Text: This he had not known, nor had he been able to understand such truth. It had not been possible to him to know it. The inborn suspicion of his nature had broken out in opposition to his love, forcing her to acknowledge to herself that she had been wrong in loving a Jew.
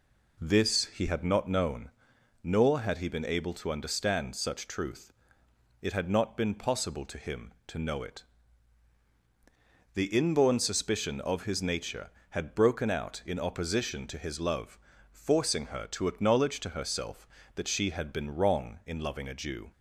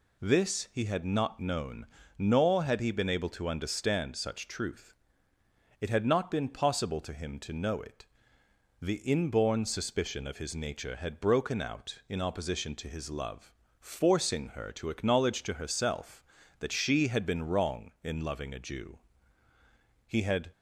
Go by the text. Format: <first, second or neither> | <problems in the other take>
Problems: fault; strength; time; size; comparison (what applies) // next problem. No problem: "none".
first | goes on to say "He had"; slight; from 20.0 s on; 0.44 s long